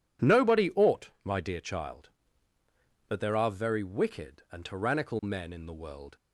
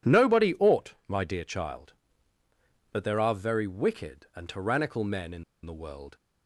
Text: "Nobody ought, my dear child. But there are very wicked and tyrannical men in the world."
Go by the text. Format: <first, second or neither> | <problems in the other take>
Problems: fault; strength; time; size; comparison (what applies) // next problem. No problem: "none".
first | pauses between "in" and "the"; slight; at 5.4 s; 0.21 s long